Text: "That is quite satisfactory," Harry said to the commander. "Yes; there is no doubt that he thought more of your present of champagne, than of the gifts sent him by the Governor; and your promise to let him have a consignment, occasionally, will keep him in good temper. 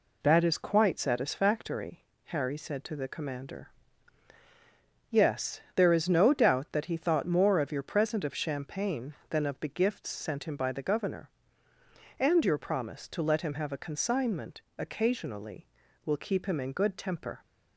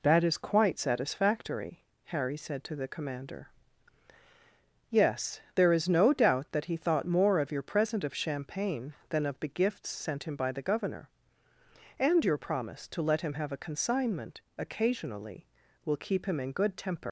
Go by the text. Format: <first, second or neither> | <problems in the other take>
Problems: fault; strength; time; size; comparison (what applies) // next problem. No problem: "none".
first | leaves "temper" unfinished; at 17.0 s; 105 ms